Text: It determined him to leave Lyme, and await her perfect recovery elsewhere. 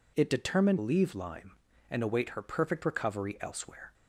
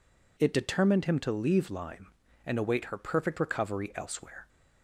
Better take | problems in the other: second | skips "him to"; at 0.7 s

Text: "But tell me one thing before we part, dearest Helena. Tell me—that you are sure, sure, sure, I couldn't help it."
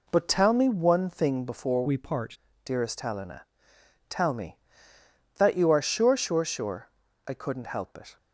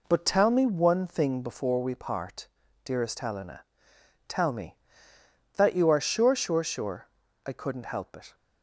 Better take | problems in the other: second | changes voice from "we" to "part"; from 1.8 to 2.3 s; 0.5 s long

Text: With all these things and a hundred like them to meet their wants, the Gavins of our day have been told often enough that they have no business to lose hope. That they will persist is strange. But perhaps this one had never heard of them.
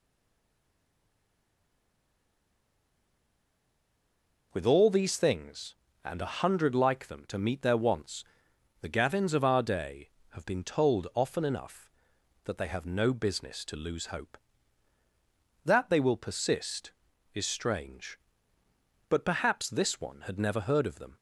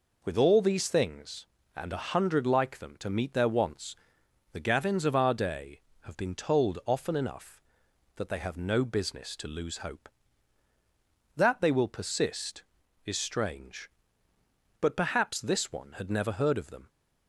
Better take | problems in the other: second | stays silent before the first word; strong; until 4.5 s; 4.5 s long

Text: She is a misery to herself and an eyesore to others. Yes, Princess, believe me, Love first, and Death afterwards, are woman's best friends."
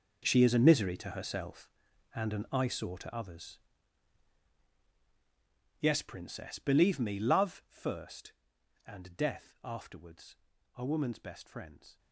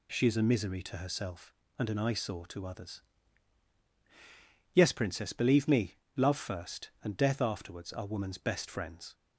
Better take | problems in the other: second | gets quieter; strong; throughout; 15.5 dB

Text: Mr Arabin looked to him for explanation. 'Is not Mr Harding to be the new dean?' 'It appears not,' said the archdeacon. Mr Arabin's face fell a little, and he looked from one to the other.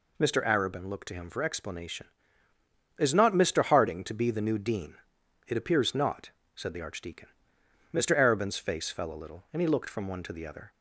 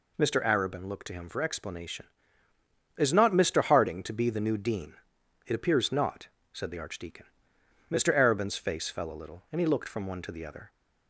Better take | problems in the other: neither | none

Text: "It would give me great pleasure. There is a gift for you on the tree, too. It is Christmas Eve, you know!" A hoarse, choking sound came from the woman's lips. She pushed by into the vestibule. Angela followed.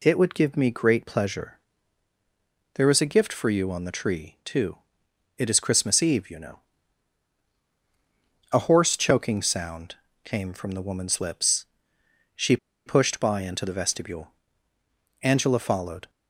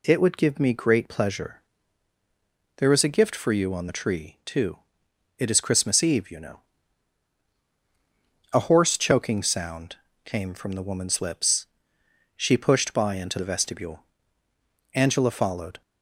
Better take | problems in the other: second | pauses between "sound" and "came"; slight; at 9.9 s; 0.30 s long; slight in the second // pauses between "She" and "pushed"; slight; at 12.5 s; 0.29 s long

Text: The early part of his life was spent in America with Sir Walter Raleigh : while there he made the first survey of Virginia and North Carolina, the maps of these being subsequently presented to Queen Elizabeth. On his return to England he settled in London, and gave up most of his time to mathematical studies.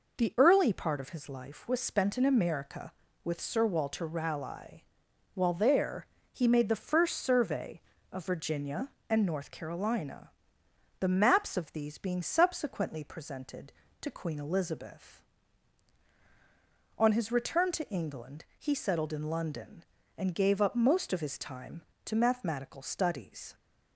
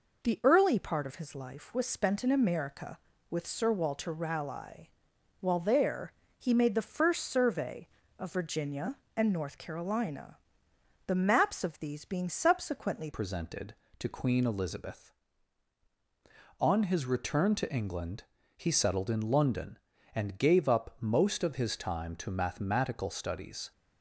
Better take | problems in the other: first | pauses between "there" and "he"; slight; at 6.1 s; 0.26 s long; slight in the first // changes voice at "presented"; from 13.1 s on; 10.6 s long // pauses between "England" and "he"; slight; at 18.2 s; 0.34 s long

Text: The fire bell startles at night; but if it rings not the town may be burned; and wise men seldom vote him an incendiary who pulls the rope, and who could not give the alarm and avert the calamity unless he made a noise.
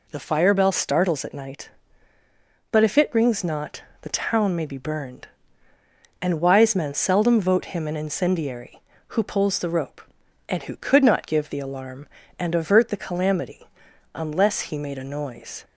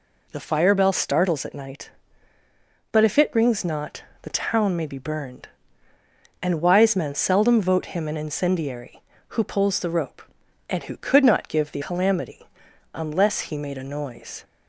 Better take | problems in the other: first | pauses between "not" and "the"; slight; at 4.0 s; 0.22 s long; slight in the first // skips "alarm and avert the"; at 11.8 s // pauses between "calamity" and "unless"; noticeable; at 12.4 s; 0.48 s long; noticeable in the first

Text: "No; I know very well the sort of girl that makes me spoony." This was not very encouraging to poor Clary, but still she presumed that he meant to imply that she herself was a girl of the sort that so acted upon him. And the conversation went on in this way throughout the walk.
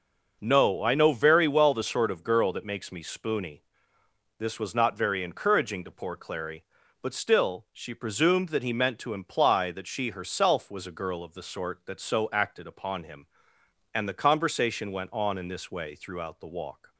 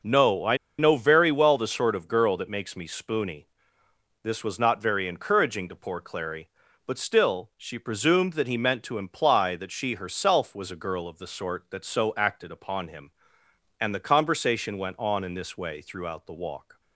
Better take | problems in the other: first | pauses between "I" and "know"; slight; at 0.5 s; 0.21 s long

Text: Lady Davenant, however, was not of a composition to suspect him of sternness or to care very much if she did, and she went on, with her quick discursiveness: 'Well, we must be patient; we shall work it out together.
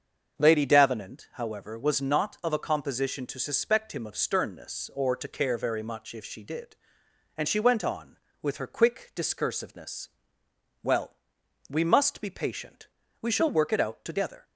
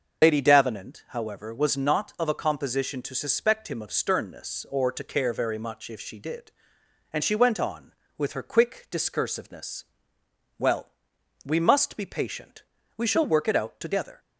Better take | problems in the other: first | loses the start of "Lady"; at 0.2 s; 85 ms // starts louder than the rest; until 1.2 s; 6.5 dB; also in the first

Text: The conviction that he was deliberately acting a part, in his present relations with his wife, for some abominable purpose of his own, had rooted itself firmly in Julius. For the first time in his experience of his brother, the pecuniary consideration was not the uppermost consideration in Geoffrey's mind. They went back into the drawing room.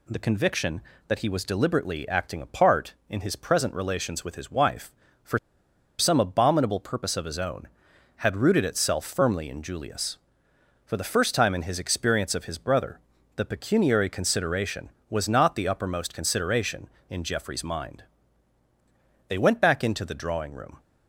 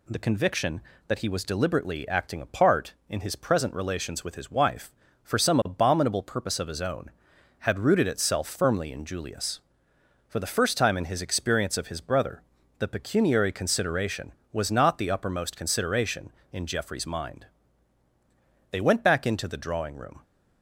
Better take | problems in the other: second | pauses between "for" and "some"; noticeable; at 5.3 s; 0.61 s long

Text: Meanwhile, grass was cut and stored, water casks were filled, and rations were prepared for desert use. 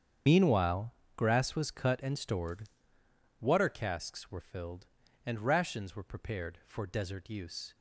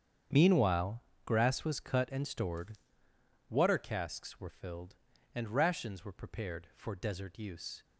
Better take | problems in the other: second | loses the start of "Meanwhile"; at 0.2 s; 45 ms // starts louder than the rest; strong; until 1.5 s; 8 dB; strong in the second

